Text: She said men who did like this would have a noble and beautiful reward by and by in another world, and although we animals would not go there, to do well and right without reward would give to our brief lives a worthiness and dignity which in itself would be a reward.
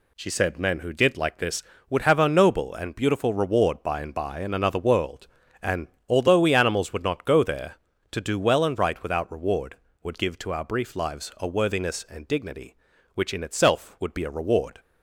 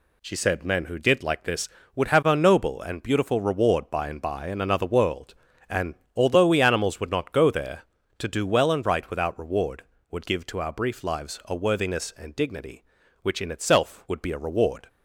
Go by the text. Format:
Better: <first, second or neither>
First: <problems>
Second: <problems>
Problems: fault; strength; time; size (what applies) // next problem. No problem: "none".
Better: neither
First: pauses between "and" and "although"; slight; at 5.8 s; 0.20 s long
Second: pauses between "and" and "although"; slight; at 5.9 s; 0.20 s long